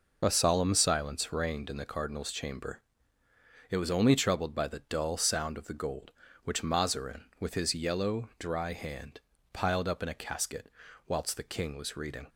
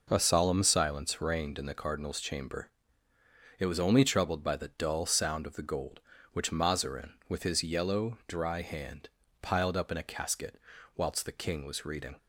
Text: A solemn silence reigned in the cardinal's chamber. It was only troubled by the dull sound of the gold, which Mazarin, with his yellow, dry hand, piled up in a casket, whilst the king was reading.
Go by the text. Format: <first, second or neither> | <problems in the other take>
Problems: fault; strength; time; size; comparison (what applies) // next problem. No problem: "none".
second | loses the start of "A"; at 0.2 s; 35 ms